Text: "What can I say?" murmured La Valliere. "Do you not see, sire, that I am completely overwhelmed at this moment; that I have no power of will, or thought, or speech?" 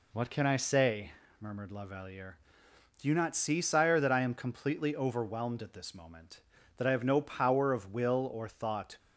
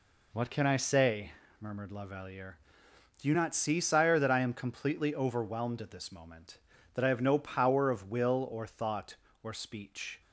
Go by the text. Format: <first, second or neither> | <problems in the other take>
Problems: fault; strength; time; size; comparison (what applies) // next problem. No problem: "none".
second | stops before "or speech"; at 8.9 s